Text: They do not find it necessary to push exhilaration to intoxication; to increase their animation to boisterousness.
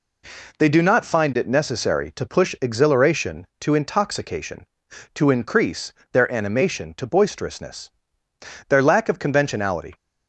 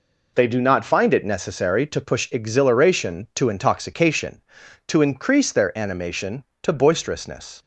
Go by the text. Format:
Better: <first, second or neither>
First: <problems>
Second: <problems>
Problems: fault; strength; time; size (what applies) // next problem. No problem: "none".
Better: second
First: pauses between "increase" and "their"; slight; at 5.9 s; 0.22 s long // goes on to say "Their lack of conventionality"; noticeable; from 8.6 s on; 1.2 s long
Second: none